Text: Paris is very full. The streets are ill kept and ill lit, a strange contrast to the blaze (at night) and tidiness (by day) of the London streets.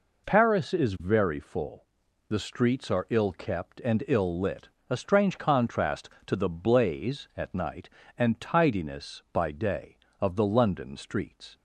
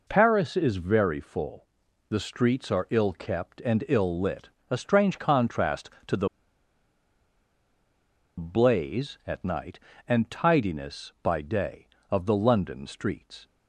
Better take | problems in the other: first | pauses between "the" and "blaze"; strong; at 6.2 s; 2.1 s long

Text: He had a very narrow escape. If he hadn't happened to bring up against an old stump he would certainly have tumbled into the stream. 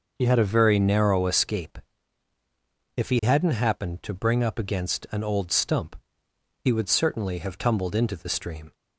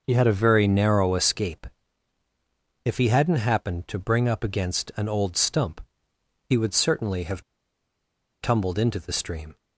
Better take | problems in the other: first | pauses between "stump" and "he"; noticeable; at 5.8 s; 0.64 s long; noticeable in the first // pauses between "have" and "tumbled"; at 7.4 s; 0.99 s long

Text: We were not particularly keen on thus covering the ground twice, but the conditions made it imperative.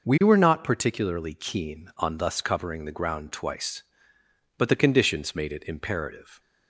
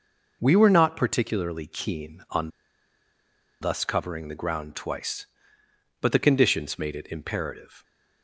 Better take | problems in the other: first | pauses between "on" and "thus"; at 2.4 s; 1.1 s long

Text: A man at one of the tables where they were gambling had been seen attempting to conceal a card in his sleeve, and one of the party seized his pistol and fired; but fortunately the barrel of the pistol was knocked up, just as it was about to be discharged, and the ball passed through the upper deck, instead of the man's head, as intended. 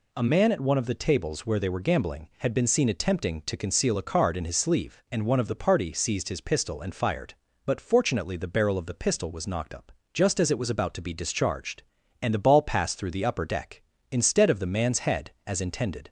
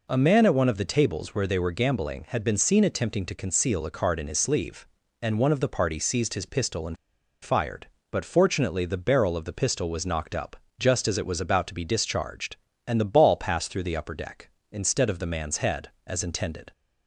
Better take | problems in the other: first | pauses between "and" and "fired"; noticeable; at 6.9 s; 0.47 s long

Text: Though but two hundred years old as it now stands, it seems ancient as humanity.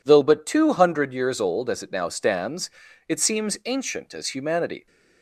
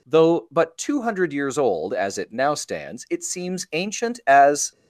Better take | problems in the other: first | stops before "humanity"; at 4.7 s

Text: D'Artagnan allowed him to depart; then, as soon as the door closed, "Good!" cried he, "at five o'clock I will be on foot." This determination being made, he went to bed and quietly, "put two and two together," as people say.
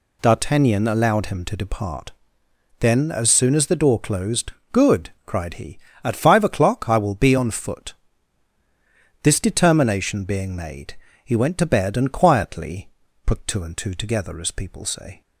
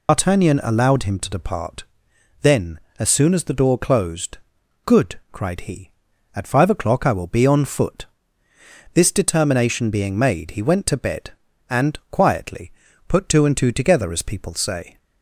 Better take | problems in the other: first | loses the start of "D'Artagnan"; at 0.0 s; 145 ms

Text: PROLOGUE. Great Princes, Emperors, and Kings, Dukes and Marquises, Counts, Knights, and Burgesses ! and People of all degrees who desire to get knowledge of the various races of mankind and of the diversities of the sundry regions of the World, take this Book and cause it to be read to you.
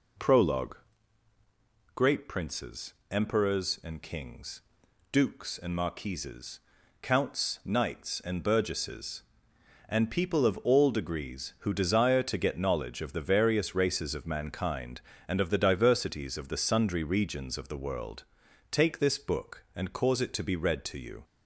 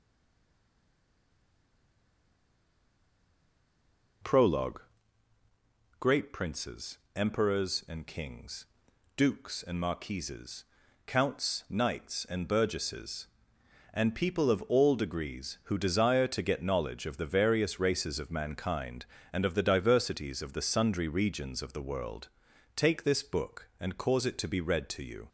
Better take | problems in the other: first | stays silent before the first word; strong; until 4.2 s; 4.2 s long

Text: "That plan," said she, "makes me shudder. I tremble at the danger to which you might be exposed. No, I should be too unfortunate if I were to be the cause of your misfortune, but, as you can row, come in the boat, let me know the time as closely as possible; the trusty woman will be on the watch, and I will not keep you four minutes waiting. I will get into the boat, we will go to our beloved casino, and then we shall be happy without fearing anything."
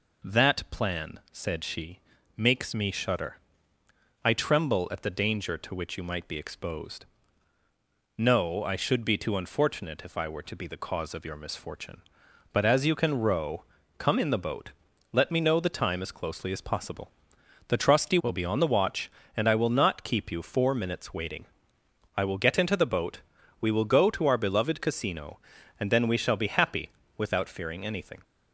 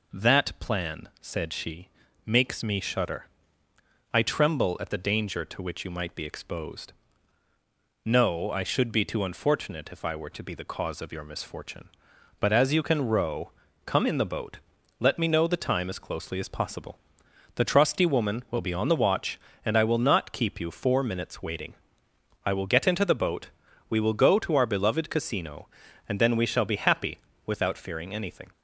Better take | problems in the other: second | skips "woman"; at 18.1 s // pauses between "happy" and "without"; slight; at 26.8 s; 0.28 s long; slight in the second

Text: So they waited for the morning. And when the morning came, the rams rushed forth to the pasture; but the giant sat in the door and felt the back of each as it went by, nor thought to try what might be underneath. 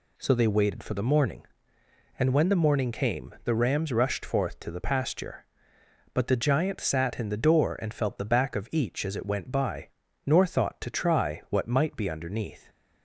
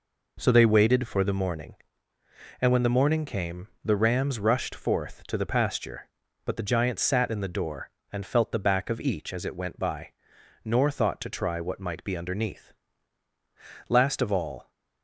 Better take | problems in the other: first | goes on to say "Last of all"; noticeable; from 13.8 s on; 0.82 s long

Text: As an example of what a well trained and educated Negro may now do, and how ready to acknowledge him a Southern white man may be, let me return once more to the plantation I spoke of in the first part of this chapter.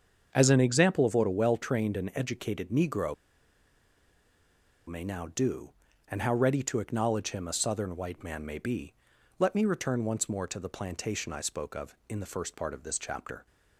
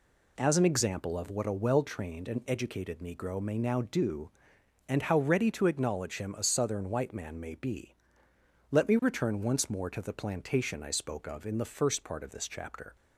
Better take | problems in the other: second | starts louder than the rest; until 1.3 s; 7 dB // pauses between "Negro" and "may"; strong; at 3.1 s; 1.7 s long

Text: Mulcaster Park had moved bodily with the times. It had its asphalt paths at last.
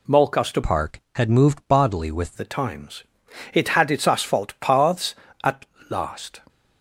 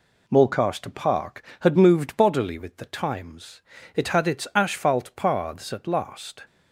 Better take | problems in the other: second | changes voice from "Park" to "with"; from 0.6 to 2.3 s; 1.7 s long // pauses between "at" and "last"; slight; at 5.6 s; 0.24 s long

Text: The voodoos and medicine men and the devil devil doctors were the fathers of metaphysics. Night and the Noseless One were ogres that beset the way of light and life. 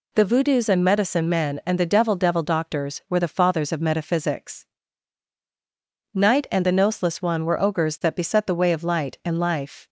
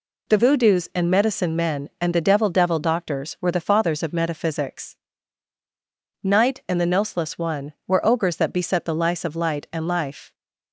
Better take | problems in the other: first | says "lice" for "way"; at 8.9 s

